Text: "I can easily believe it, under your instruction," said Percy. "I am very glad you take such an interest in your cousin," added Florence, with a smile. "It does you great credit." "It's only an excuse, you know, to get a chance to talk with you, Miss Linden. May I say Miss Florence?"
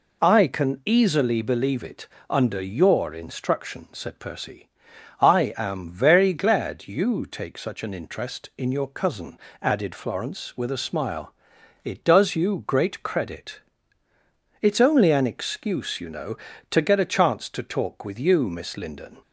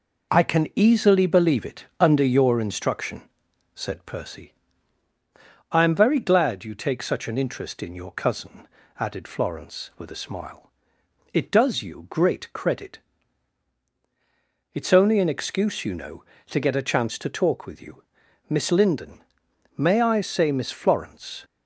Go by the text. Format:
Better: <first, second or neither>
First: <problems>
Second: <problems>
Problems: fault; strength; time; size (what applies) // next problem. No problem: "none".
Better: second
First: stops before "May I say Miss Florence"; at 19.2 s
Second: none